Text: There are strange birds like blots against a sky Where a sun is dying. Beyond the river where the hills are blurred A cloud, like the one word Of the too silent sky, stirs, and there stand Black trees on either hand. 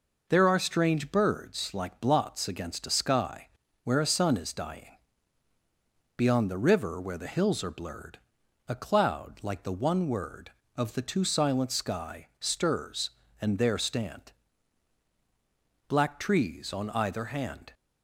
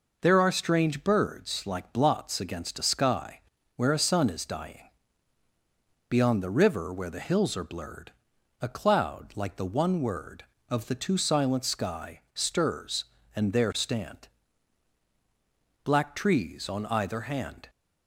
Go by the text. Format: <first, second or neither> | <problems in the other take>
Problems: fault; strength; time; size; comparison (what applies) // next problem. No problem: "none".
neither | pauses between "sky" and "Where"; slight; the same in both // pauses between "blurred" and "A"; noticeable; the same in both // pauses between "stand" and "Black"; strong; the same in both